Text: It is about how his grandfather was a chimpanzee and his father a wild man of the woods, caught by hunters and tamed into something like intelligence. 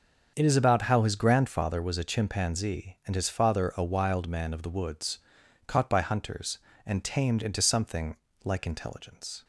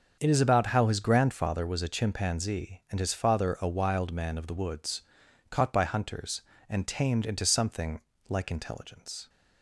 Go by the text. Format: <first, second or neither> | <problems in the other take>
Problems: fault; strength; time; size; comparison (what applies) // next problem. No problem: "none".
neither | starts louder than the rest; the same in both // pauses between "something" and "like"; slight; the same in both